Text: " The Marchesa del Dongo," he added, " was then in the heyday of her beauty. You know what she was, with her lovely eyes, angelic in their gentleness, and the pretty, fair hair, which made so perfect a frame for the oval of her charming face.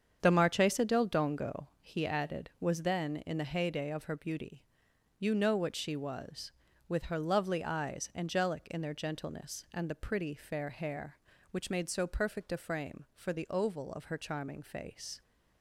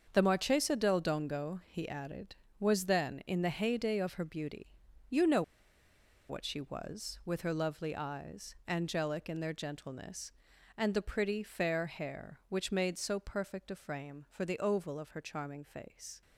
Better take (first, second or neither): first